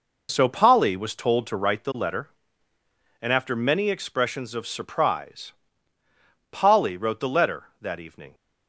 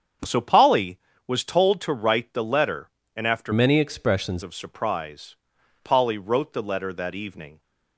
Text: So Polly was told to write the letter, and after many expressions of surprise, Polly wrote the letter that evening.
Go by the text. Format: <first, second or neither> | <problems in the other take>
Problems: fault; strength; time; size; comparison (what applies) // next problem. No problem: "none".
first | starts louder than the rest; strong; until 1.5 s; 7.5 dB // changes voice from "many" to "expressions"; from 3.5 to 4.4 s; 0.9 s long